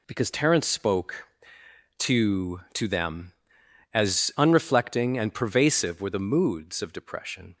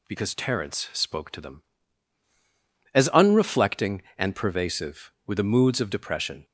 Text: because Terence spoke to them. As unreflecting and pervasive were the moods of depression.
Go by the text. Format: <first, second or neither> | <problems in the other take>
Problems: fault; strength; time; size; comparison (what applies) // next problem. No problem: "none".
second | says "to" twice; at 2.7 s